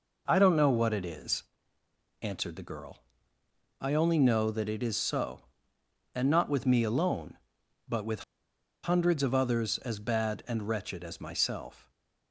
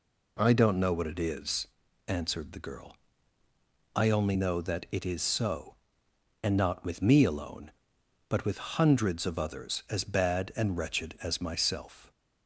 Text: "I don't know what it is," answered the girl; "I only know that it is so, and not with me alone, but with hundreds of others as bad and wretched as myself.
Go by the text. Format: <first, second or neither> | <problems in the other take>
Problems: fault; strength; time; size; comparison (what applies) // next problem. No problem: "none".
second | pauses between "with" and "hundreds"; noticeable; at 8.2 s; 0.61 s long